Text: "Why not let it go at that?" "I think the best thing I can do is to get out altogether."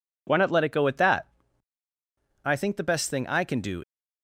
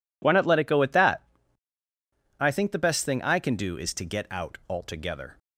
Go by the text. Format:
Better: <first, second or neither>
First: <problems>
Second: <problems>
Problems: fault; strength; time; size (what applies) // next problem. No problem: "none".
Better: second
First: stops before "is to get out altogether"; at 3.8 s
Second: none